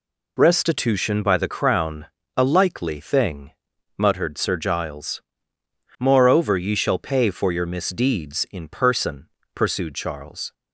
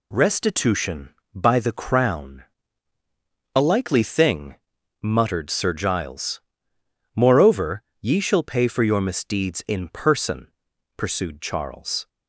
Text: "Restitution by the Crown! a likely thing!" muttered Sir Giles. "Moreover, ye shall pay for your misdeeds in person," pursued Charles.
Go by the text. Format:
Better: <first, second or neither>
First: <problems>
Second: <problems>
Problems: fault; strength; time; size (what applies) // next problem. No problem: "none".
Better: neither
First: none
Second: none